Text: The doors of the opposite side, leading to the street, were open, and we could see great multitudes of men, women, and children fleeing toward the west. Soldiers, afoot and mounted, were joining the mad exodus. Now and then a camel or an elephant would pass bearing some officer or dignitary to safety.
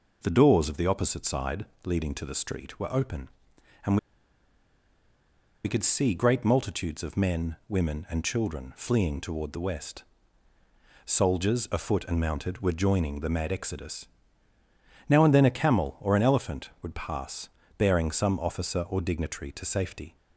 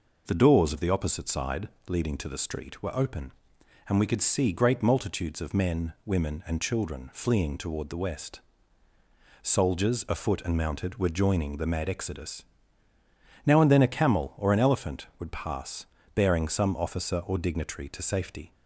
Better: second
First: pauses between "and" and "we"; strong; at 3.9 s; 1.6 s long // pauses between "pass" and "bearing"; slight; at 17.4 s; 0.30 s long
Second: pauses between "pass" and "bearing"; slight; at 15.8 s; 0.30 s long

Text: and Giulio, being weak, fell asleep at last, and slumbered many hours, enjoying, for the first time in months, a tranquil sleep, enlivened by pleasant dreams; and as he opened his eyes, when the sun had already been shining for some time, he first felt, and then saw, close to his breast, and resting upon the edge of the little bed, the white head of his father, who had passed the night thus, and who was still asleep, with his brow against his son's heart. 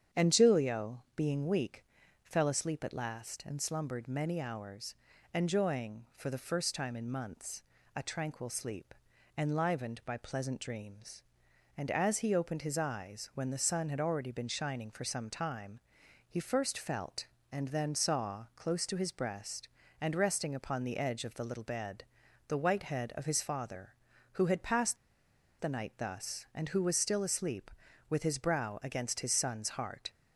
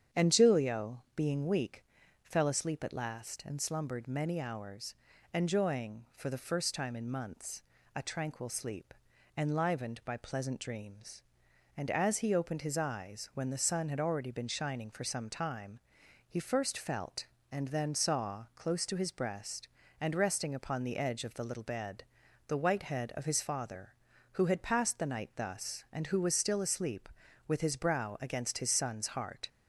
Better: second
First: starts louder than the rest; strong; until 1.2 s; 8.5 dB // pauses between "passed" and "the"; noticeable; at 24.9 s; 0.63 s long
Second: starts louder than the rest; strong; until 1.2 s; 8.5 dB

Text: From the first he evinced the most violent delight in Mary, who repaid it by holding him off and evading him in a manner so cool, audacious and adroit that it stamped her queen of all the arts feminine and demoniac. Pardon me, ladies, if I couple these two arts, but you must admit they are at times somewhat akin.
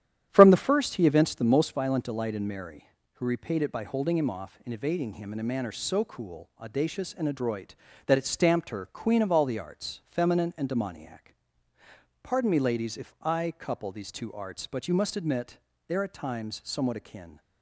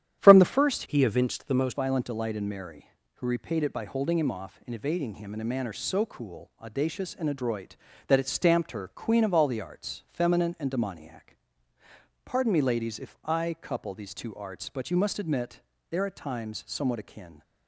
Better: first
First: starts louder than the rest; strong; until 1.3 s; 10.5 dB // pauses between "admit" and "they"; slight; at 15.5 s; 0.30 s long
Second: starts louder than the rest; strong; until 1.2 s; 10.5 dB // changes voice from "he" to "most"; from 0.8 to 1.7 s; 0.9 s long // pauses between "admit" and "they"; slight; at 15.5 s; 0.30 s long

